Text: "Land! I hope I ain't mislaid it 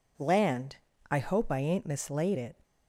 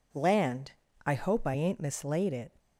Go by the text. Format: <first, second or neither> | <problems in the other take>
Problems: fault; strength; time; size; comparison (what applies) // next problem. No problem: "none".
neither | none